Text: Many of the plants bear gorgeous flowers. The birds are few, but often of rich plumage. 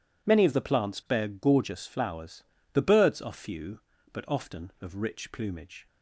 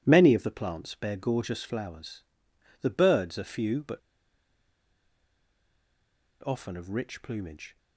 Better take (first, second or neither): first